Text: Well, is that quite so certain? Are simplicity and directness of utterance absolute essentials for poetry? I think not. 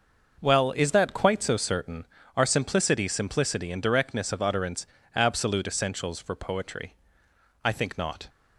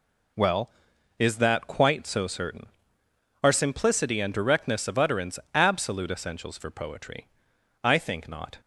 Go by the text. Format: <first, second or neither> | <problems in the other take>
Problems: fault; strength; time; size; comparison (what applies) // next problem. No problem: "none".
second | starts louder than the rest; noticeable; until 1.4 s; 6 dB // says "simplicity" twice; at 3.0 s // pauses between "utterance" and "absolute"; slight; at 4.8 s; 0.26 s long; slight in the second